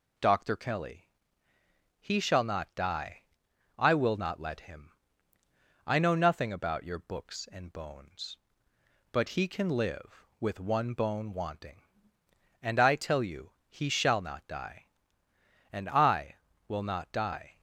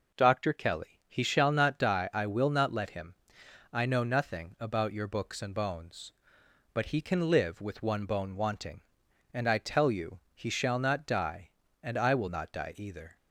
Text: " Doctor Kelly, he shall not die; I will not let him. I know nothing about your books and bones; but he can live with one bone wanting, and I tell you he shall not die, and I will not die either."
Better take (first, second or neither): second